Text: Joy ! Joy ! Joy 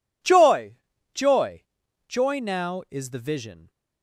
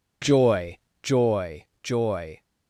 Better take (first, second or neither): second